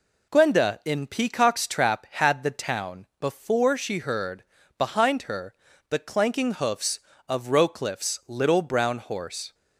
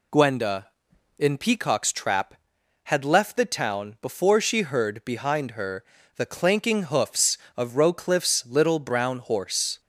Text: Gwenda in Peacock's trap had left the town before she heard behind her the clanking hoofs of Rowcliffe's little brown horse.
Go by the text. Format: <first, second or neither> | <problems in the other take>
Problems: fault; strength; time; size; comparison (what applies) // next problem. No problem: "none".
second | skips "left"; at 2.4 s // pauses between "heard" and "behind"; slight; at 4.4 s; 0.32 s long // pauses between "her" and "the"; slight; at 5.5 s; 0.34 s long; slight in the second